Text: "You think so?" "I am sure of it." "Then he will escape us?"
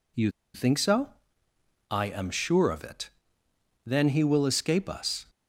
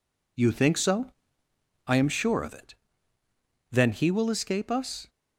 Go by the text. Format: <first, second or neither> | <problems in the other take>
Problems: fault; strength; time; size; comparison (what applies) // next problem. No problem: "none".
second | pauses between "You" and "think"; slight; at 0.2 s; 0.24 s long